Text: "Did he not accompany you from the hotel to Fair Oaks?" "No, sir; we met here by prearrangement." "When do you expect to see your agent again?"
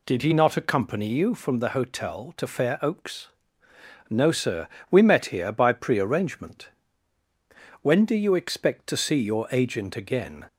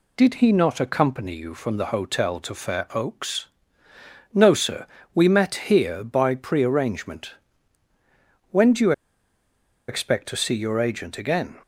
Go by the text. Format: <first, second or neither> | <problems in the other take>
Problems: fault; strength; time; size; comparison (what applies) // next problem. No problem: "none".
first | pauses between "you" and "expect"; noticeable; at 8.9 s; 0.96 s long